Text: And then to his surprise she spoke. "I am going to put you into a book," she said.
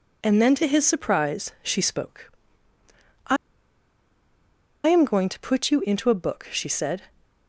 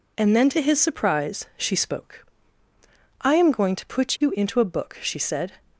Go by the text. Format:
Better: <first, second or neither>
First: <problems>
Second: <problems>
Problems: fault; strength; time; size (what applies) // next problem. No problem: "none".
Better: second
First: pauses between "I" and "am"; strong; at 3.3 s; 1.5 s long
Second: none